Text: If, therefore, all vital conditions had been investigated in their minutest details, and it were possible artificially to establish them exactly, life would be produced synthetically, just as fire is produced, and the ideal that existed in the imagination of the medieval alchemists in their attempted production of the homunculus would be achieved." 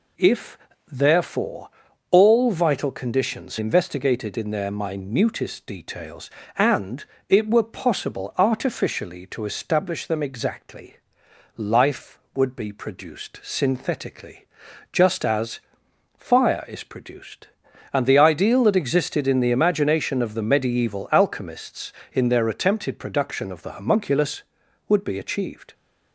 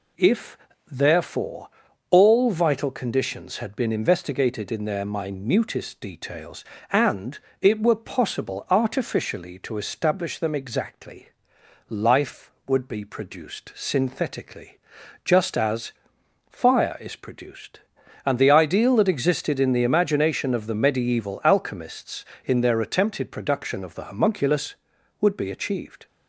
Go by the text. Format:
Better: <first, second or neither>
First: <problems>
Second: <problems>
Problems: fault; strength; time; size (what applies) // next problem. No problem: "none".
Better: second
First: skips "had been"; at 3.5 s // pauses between "and" and "it"; slight; at 7.0 s; 0.26 s long // pauses between "as" and "fire"; noticeable; at 15.5 s; 0.56 s long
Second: pauses between "and" and "it"; slight; at 7.3 s; 0.24 s long // pauses between "as" and "fire"; noticeable; at 15.9 s; 0.56 s long